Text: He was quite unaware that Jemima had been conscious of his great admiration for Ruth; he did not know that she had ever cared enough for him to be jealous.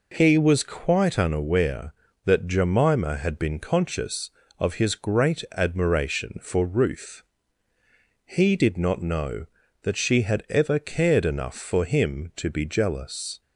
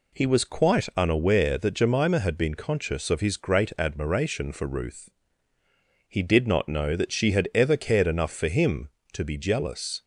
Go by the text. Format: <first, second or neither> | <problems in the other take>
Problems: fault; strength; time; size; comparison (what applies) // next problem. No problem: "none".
neither | none